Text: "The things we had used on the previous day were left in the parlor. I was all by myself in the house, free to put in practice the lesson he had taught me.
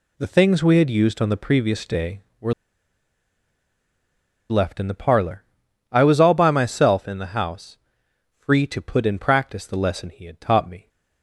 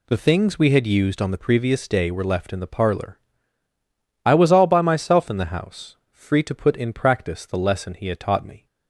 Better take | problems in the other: second | pauses between "were" and "left"; strong; at 2.5 s; 1.9 s long

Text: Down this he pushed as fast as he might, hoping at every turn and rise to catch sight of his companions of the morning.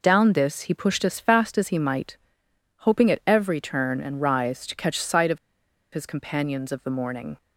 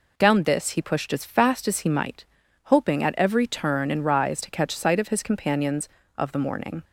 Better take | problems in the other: second | pauses between "of" and "his"; noticeable; at 5.3 s; 0.56 s long

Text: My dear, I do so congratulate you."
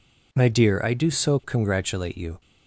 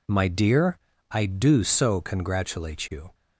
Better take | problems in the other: neither | none

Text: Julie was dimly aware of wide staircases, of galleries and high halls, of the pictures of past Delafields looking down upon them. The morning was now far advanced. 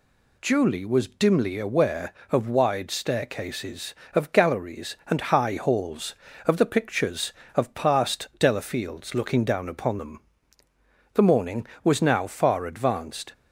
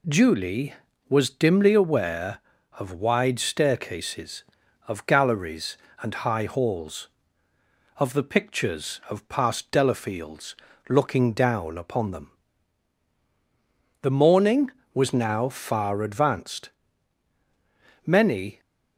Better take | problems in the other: first | pauses between "Delafields" and "looking"; slight; at 10.5 s; 0.34 s long // goes on to say "Many"; from 18.0 s on; 0.54 s long

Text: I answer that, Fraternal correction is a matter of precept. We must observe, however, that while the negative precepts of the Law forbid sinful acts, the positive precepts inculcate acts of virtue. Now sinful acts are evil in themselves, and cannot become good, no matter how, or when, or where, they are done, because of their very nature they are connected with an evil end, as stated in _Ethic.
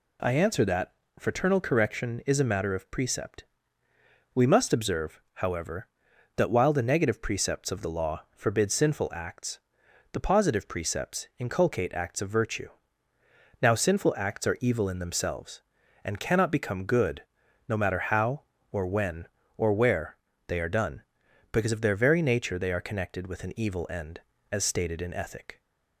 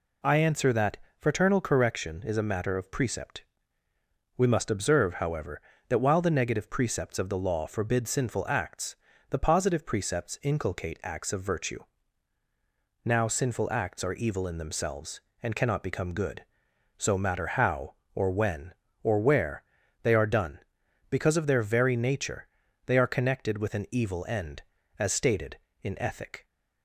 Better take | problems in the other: first | says "so" for "no"; at 16.9 s // pauses between "nature" and "they"; at 22.4 s; 0.40 s long

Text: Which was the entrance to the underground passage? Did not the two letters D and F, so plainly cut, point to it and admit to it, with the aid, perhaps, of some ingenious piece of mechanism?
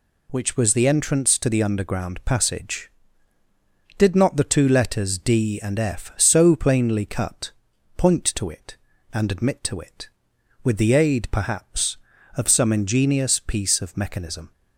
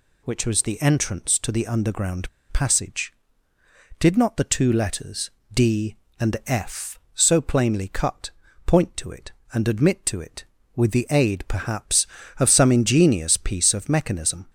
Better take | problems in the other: first | pauses between "underground" and "passage"; slight; at 2.2 s; 0.21 s long // pauses between "letters" and "D"; slight; at 5.2 s; 0.24 s long

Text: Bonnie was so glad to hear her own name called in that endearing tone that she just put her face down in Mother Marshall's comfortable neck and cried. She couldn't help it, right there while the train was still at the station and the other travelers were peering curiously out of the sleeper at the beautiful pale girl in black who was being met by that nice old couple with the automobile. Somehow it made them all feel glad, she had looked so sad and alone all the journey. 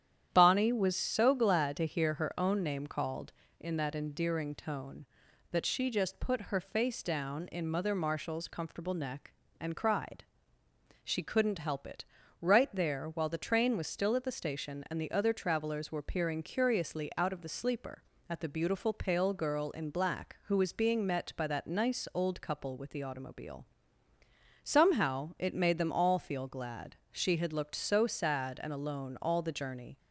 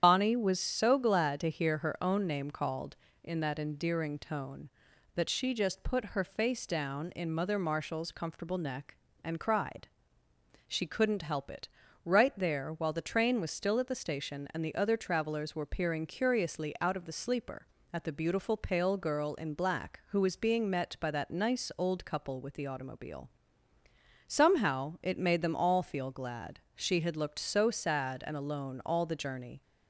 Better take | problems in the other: first | loses the start of "Bonnie"; at 0.0 s; 75 ms // starts louder than the rest; strong; until 1.0 s; 9 dB; strong in the first

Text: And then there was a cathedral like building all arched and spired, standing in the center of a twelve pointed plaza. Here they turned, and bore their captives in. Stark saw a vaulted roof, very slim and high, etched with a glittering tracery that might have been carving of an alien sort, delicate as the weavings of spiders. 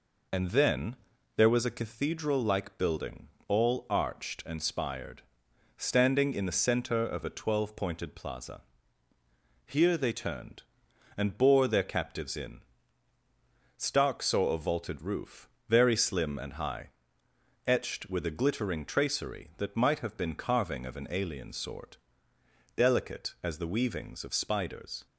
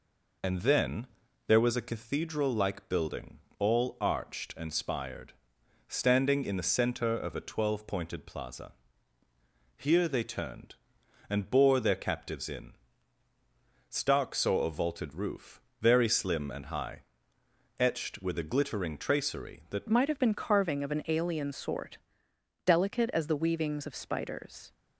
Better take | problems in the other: first | pauses between "then" and "there"; at 1.0 s; 0.42 s long; also in the first // pauses between "building" and "all"; slight; at 3.3 s; 0.18 s long; slight in the first // changes voice at "might"; from 19.8 s on; 4.9 s long

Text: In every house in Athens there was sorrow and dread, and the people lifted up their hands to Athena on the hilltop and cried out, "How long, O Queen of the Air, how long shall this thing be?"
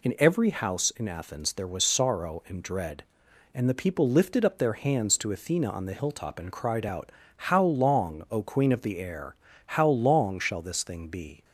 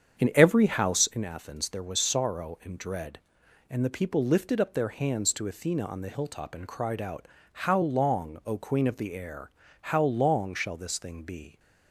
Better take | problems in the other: first | starts louder than the rest; strong; until 1.3 s; 8 dB

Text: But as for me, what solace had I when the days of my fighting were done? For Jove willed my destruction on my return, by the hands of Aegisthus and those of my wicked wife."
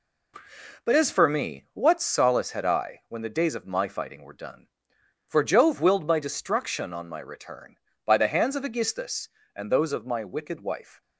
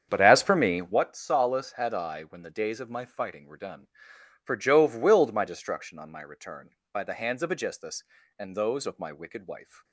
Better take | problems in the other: first | starts louder than the rest; strong; until 1.1 s; 8 dB

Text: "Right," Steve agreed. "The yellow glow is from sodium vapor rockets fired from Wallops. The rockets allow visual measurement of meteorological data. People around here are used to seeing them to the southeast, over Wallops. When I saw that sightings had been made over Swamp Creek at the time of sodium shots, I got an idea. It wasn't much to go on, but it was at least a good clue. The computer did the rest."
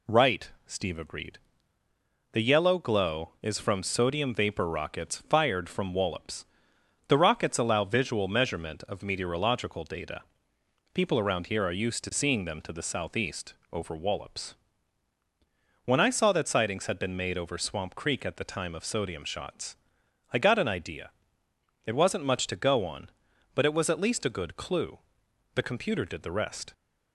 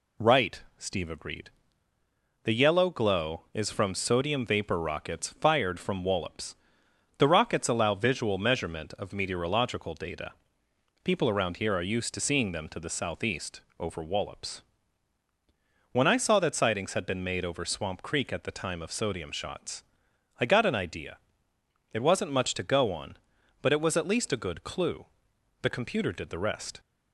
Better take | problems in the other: neither | none

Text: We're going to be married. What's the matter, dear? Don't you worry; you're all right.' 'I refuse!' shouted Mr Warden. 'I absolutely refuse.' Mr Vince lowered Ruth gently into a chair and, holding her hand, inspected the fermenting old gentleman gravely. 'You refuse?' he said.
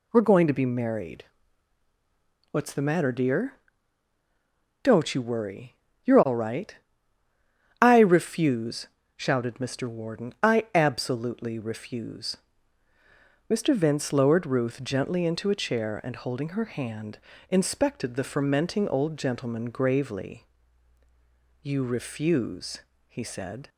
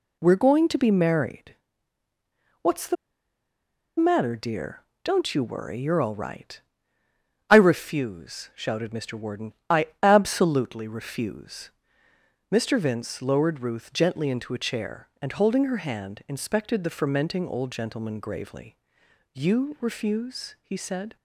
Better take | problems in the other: first | pauses between "the" and "matter"; at 2.9 s; 1.0 s long

